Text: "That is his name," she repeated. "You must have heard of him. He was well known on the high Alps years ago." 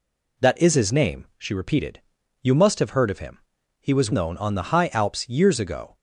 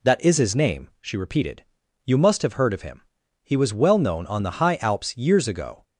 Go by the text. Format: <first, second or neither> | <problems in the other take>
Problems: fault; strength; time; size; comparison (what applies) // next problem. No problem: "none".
second | skips "well"; at 4.1 s